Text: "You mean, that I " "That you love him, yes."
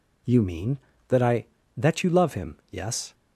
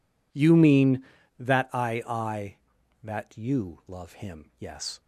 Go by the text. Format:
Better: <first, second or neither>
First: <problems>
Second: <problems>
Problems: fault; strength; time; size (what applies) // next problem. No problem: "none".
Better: first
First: none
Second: says "I" twice; at 2.0 s